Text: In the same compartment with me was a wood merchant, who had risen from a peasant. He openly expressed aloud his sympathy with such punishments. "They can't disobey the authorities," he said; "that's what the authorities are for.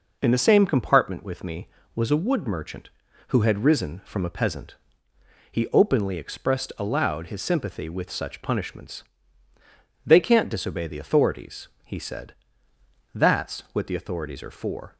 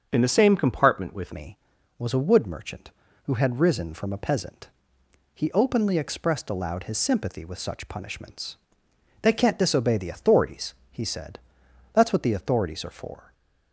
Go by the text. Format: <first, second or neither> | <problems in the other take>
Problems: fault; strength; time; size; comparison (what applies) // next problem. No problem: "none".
first | starts louder than the rest; until 1.1 s; 7 dB // changes voice at "me"; from 1.3 s on; 12.0 s long